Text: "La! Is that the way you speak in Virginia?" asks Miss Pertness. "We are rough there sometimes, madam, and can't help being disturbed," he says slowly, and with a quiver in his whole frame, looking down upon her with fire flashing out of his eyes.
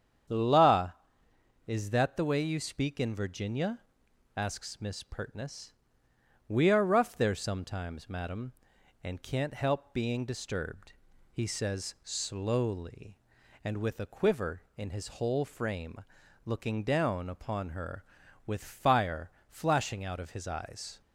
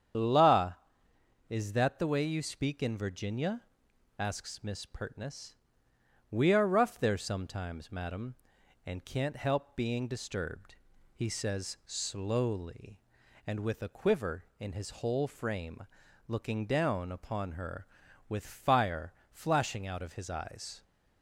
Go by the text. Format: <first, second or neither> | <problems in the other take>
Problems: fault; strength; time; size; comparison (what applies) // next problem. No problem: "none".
first | loses the start of "La"; at 0.1 s; 30 ms // starts louder than the rest; strong; until 1.9 s; 8.5 dB; strong in the first // pauses between "fire" and "flashing"; slight; at 19.1 s; 0.18 s long; slight in the first